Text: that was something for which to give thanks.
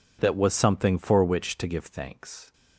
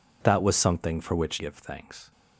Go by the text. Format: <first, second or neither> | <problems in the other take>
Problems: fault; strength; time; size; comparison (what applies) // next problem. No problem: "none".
first | skips "to"; at 1.3 s